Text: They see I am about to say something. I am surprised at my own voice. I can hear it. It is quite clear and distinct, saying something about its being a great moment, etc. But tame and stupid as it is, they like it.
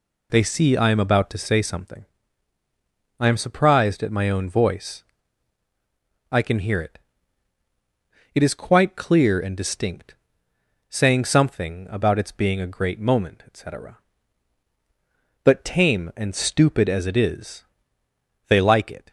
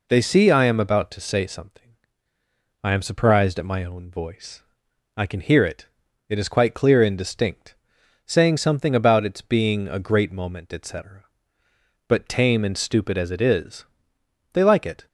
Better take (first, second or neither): neither